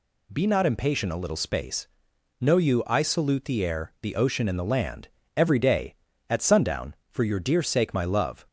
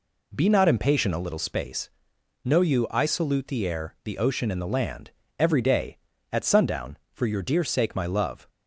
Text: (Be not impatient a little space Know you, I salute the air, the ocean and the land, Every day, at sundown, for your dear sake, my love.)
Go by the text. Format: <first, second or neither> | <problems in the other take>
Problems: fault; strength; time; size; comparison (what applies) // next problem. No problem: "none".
first | starts louder than the rest; slight; until 1.4 s; 3 dB // pauses between "space" and "Know"; noticeable; at 1.9 s; 0.52 s long; noticeable in the first